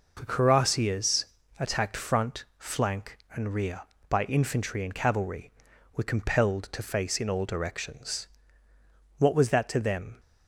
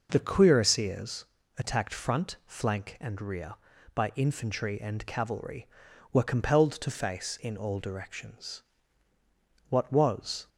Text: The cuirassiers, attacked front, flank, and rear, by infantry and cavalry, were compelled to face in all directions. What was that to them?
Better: first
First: none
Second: stops before "that to them"; at 10.4 s

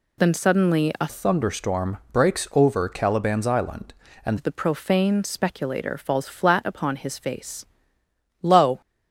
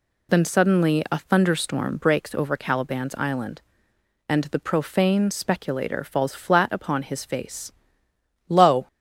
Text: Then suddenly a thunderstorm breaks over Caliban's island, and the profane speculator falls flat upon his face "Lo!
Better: second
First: changes voice from "thunderstorm" to "and"; from 1.0 to 4.3 s; 3.3 s long // pauses between "face" and "Lo"; noticeable; at 7.6 s; 0.78 s long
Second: pauses between "face" and "Lo"; noticeable; at 7.7 s; 0.78 s long

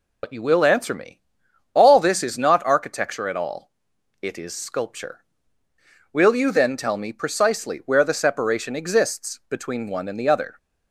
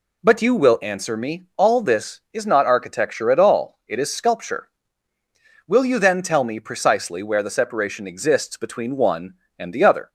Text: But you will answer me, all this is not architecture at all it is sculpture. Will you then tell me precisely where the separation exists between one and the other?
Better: second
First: loses the start of "But"; at 0.2 s; 60 ms // pauses between "all" and "it"; noticeable; at 3.7 s; 0.50 s long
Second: none

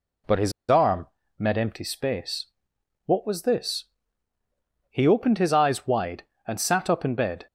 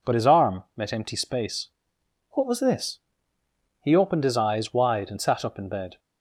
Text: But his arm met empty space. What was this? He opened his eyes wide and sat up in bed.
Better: second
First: pauses between "his" and "arm"; slight; at 0.5 s; 0.18 s long // pauses between "arm" and "met"; slight; at 1.0 s; 0.32 s long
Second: none

